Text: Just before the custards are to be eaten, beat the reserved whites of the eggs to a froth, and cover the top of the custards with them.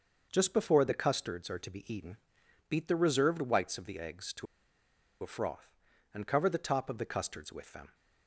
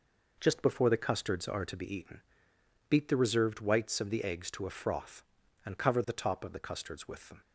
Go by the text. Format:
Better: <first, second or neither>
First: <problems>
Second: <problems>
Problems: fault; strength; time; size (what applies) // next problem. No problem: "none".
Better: second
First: starts louder than the rest; noticeable; until 1.3 s; 6 dB // pauses between "to" and "a"; noticeable; at 4.4 s; 0.76 s long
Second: none